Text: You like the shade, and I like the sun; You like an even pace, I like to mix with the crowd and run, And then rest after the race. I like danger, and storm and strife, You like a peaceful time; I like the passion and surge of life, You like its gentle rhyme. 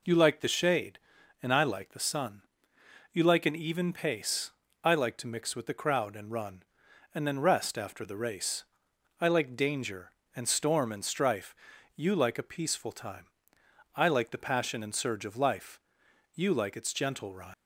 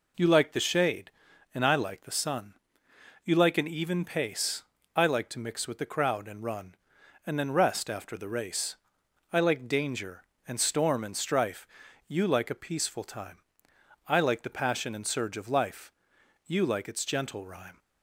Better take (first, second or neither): second